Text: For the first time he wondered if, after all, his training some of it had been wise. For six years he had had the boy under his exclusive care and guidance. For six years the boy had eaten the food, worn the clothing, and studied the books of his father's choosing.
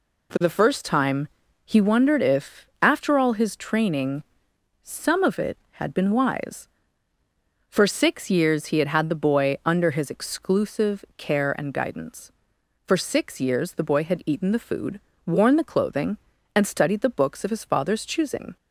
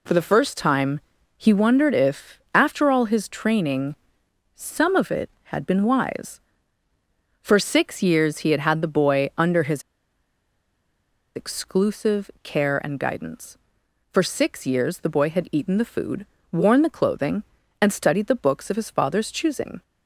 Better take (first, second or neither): first